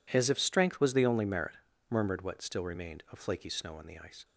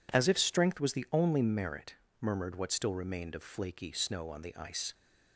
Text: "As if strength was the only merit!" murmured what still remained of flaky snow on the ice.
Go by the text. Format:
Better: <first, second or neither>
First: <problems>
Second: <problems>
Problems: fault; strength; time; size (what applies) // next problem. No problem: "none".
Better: neither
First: none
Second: none